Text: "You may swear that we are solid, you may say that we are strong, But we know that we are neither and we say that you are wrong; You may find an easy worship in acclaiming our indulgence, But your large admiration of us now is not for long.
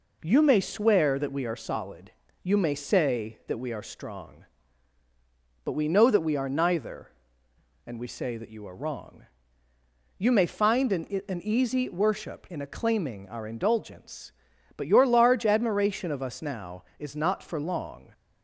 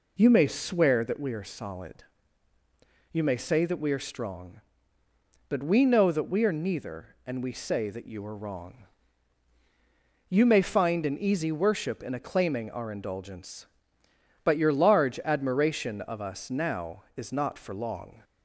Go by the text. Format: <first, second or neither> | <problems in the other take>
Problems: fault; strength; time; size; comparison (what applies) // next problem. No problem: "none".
second | says "an" twice; at 11.2 s